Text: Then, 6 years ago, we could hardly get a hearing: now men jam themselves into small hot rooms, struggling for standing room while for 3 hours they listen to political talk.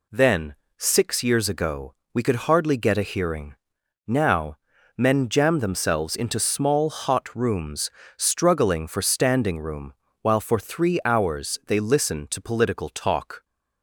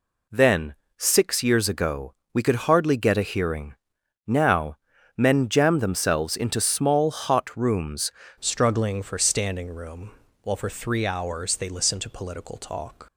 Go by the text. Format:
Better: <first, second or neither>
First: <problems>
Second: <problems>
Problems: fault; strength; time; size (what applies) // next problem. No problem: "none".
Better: first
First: pauses between "now" and "men"; at 4.5 s; 0.42 s long // pauses between "room" and "while"; slight; at 9.9 s; 0.28 s long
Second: pauses between "now" and "men"; at 4.7 s; 0.42 s long // changes voice at "struggling"; from 8.3 s on; 4.7 s long // pauses between "room" and "while"; slight; at 10.1 s; 0.32 s long